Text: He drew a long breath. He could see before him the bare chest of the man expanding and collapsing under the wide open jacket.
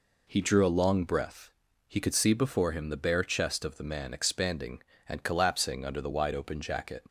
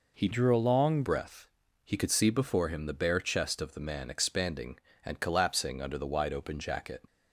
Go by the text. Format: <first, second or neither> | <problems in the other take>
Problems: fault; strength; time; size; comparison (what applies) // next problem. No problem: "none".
first | changes voice from "drew" to "long"; from 0.3 to 1.0 s; 0.7 s long